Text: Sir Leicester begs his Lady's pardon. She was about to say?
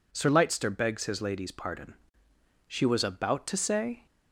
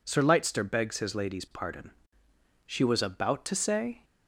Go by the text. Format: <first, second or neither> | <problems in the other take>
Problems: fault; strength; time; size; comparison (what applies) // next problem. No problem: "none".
neither | none